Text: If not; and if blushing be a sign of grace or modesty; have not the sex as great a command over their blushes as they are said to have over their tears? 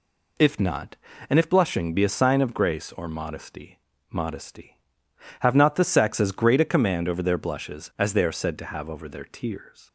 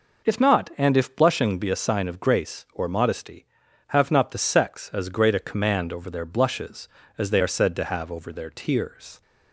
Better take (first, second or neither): second